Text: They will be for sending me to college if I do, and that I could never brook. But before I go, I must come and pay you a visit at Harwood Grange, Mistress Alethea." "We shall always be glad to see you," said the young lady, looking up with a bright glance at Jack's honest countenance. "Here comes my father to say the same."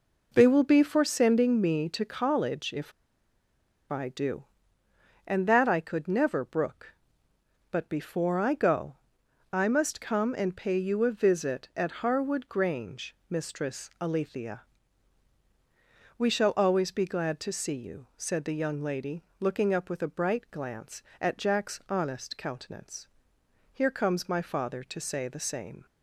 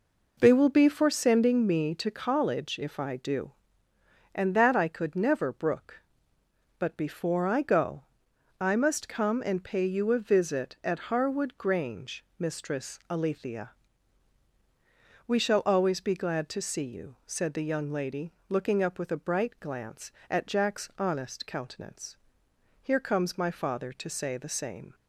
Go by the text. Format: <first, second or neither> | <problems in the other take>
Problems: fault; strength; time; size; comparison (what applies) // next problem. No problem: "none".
second | pauses between "if" and "I"; at 2.9 s; 0.99 s long